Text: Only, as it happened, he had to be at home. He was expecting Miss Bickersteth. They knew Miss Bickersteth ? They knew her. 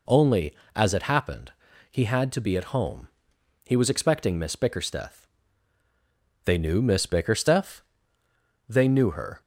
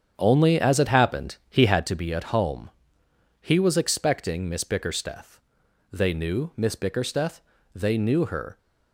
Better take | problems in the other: first | starts louder than the rest; strong; until 2.0 s; 8 dB

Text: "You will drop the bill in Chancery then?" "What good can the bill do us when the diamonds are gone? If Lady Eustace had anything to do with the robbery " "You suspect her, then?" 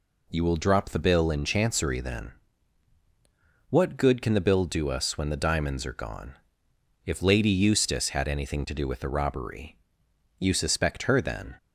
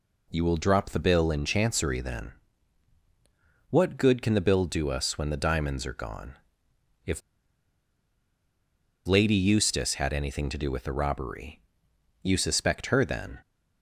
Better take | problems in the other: first | pauses between "If" and "Lady"; strong; at 7.2 s; 1.8 s long

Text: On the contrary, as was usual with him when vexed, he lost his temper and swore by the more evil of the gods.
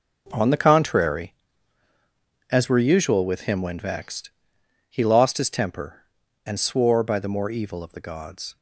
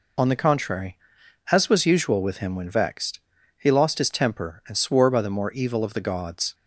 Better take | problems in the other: second | says "were" for "was"; at 2.6 s

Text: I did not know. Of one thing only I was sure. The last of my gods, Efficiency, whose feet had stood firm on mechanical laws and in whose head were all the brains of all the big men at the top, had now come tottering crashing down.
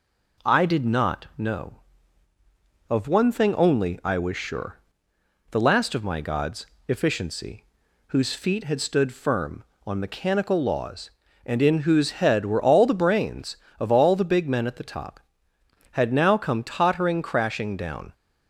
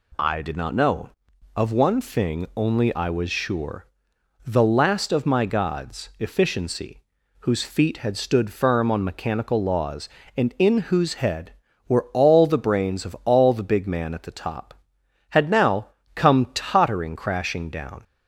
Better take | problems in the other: first | says "man" for "men"; at 13.8 s // pauses between "now" and "come"; slight; at 15.8 s; 0.28 s long

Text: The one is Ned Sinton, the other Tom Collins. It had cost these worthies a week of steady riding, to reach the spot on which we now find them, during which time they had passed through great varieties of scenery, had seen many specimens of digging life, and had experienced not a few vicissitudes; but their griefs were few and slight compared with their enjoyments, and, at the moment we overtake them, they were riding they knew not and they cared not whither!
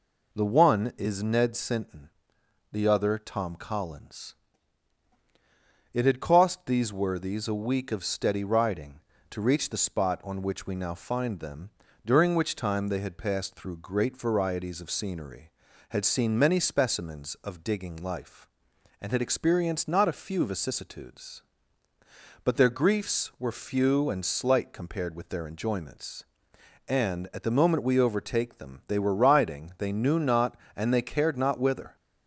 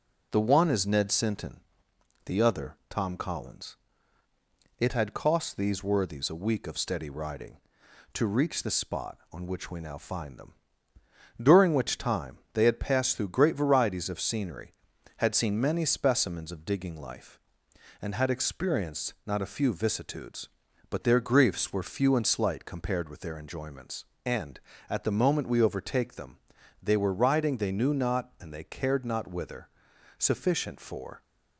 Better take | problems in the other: first | pauses between "time" and "they"; slight; at 12.3 s; 0.16 s long // goes on to say "Sufficient for"; noticeable; from 30.1 s on; 1.0 s long

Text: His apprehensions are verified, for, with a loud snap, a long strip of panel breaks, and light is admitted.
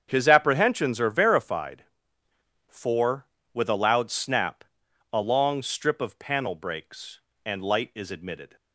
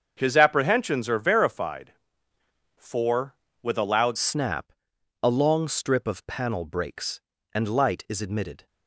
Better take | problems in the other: first | starts louder than the rest; until 1.1 s; 7 dB; strong in the first // changes voice at "snap"; from 4.1 s on; 4.5 s long

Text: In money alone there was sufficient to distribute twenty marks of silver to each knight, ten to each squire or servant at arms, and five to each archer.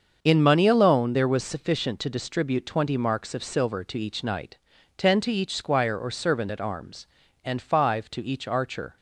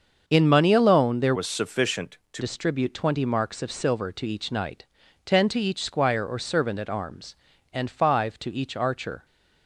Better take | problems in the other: first | starts louder than the rest; until 1.2 s; 7 dB; also in the first // changes voice from "was" to "to"; from 1.3 to 2.4 s; 1.1 s long

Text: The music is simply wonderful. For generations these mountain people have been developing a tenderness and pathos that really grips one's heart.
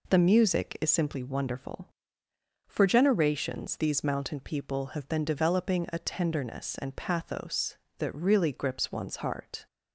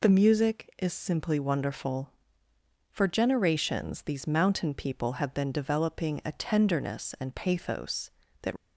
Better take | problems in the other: first | stops before "really grips one's heart"; at 8.5 s

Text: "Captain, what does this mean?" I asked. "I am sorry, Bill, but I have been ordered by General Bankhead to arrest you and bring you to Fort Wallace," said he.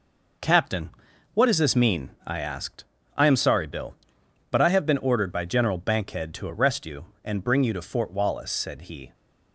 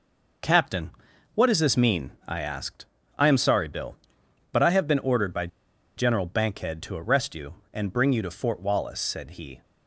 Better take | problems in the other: first | pauses between "by" and "General"; noticeable; at 5.4 s; 0.49 s long

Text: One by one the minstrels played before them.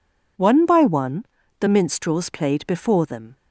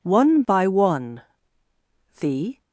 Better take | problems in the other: first | pauses between "one" and "the"; noticeable; at 1.2 s; 0.98 s long; slight in the first // stops before "minstrels played before them"; at 2.6 s

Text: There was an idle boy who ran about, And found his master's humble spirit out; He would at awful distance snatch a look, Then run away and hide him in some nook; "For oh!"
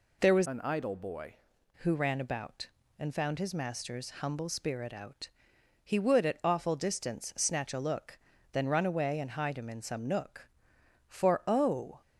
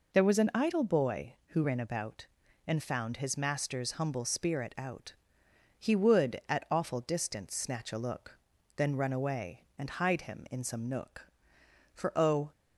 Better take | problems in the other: second | changes voice from "an" to "boy"; from 0.4 to 1.3 s; 0.9 s long

